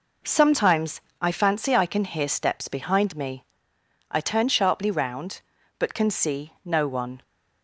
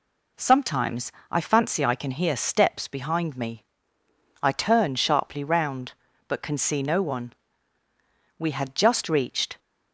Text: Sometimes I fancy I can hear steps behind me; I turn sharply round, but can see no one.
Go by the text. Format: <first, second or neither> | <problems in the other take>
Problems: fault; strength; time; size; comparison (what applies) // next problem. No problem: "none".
first | pauses between "Sometimes" and "I"; slight; at 1.1 s; 0.18 s long; slight in the first // goes on to say "We had just reached"; noticeable; from 8.3 s on; 1.2 s long